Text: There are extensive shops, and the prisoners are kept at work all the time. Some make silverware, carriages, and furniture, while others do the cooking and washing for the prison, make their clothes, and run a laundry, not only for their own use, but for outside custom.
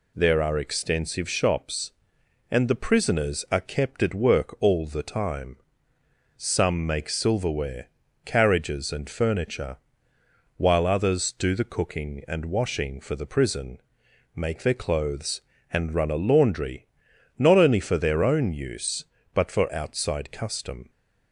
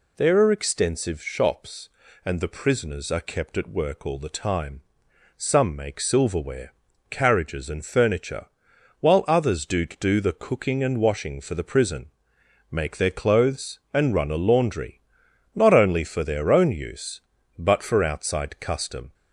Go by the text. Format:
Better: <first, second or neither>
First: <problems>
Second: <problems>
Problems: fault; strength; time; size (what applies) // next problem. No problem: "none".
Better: first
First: none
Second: says "do" twice; at 9.8 s